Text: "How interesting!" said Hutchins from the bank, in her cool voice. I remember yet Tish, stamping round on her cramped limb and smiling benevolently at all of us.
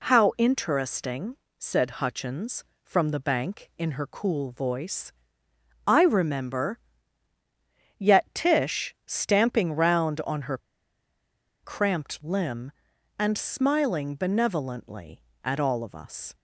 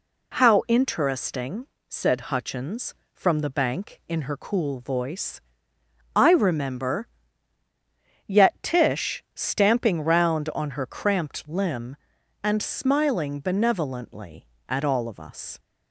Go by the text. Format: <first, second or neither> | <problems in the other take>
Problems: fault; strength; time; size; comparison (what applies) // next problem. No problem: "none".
second | pauses between "remember" and "yet"; at 6.8 s; 1.1 s long; also in the second // pauses between "her" and "cramped"; at 10.5 s; 1.0 s long